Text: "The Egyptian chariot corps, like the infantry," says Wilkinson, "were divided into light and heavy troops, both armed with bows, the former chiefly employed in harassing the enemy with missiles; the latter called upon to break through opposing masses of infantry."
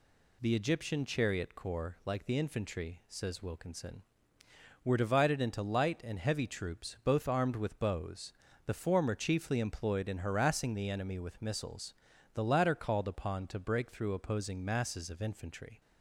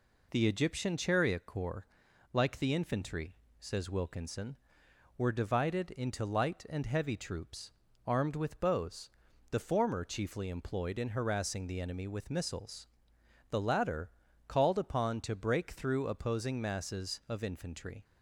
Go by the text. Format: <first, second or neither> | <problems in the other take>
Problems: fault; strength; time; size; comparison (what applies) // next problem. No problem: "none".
first | skips "both"; at 7.8 s // pauses between "latter" and "called"; at 14.0 s; 0.38 s long